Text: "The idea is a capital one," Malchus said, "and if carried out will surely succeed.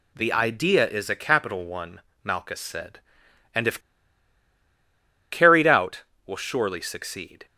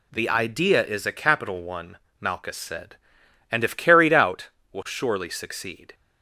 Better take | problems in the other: second | pauses between "if" and "carried"; strong; at 3.7 s; 1.5 s long

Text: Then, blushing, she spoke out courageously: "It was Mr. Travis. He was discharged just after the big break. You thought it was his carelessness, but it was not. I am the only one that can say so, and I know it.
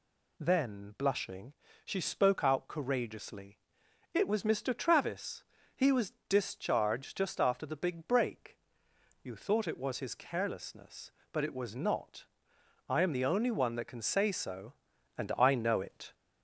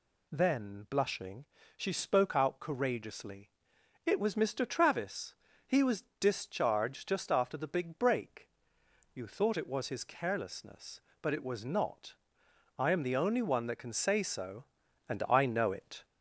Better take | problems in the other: neither | pauses between "was" and "discharged"; slight; the same in both

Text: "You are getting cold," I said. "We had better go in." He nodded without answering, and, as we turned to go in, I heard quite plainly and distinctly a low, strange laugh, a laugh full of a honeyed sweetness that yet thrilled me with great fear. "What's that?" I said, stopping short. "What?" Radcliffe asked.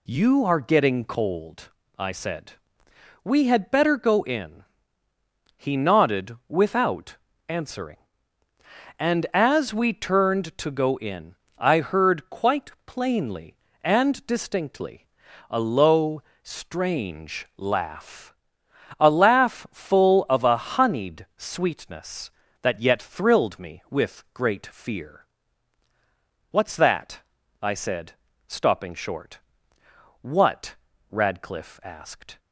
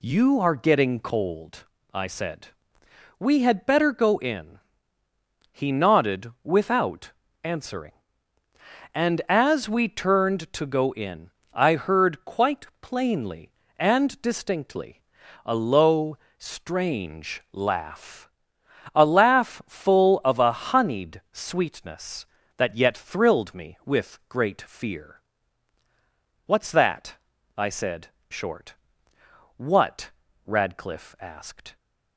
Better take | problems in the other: first | pauses between "without" and "answering"; slight; at 7.1 s; 0.32 s long; slight in the first // pauses between "quite" and "plainly"; slight; at 12.6 s; 0.16 s long; slight in the first // pauses between "distinctly" and "a"; at 15.0 s; 0.42 s long; also in the first // skips "stopping"; at 28.1 s

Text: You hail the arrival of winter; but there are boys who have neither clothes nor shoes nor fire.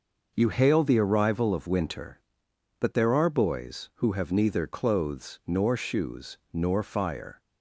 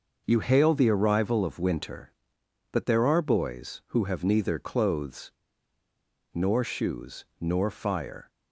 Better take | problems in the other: first | pauses between "clothes" and "nor"; at 5.3 s; 1.0 s long // pauses between "shoes" and "nor"; slight; at 7.2 s; 0.16 s long; slight in the first

